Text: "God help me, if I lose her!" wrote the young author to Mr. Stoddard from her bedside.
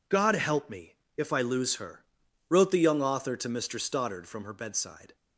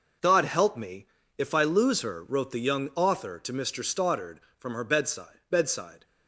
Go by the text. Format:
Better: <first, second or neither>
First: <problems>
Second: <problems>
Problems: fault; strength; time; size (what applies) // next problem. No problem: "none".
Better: first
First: none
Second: says "bedside" twice; at 5.4 s